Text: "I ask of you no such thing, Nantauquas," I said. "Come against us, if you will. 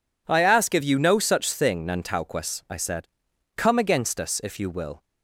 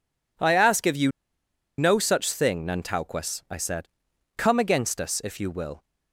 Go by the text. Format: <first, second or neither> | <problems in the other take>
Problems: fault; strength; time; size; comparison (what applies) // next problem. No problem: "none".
first | pauses between "you" and "no"; noticeable; at 1.1 s; 0.67 s long